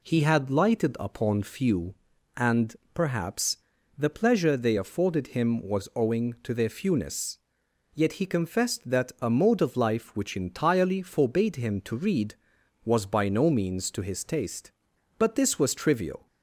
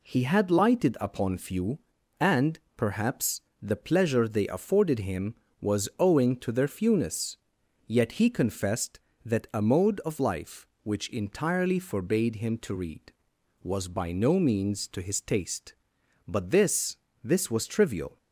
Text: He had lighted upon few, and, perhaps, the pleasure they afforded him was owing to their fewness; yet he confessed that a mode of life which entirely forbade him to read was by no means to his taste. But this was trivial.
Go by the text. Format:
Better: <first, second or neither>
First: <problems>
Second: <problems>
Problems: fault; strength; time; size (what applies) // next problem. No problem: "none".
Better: first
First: none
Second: says "this" twice; at 17.2 s